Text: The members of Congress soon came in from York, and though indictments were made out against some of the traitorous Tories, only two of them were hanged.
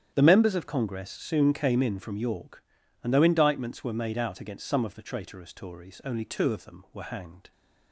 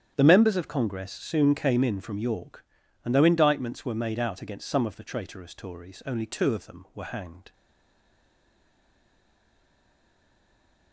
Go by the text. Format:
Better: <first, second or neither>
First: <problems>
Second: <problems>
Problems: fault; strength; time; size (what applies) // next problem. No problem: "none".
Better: first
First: starts louder than the rest; strong; until 1.1 s; 9.5 dB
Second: starts louder than the rest; strong; until 1.1 s; 9.5 dB // stays silent after the last word; strong; from 7.5 s on; 3.4 s long